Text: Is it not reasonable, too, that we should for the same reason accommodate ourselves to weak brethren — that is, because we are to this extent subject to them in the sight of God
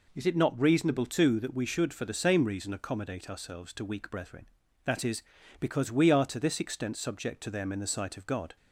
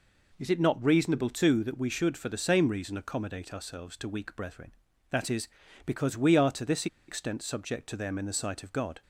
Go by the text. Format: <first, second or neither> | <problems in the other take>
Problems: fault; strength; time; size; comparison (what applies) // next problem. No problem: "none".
first | pauses between "this" and "extent"; slight; at 6.8 s; 0.21 s long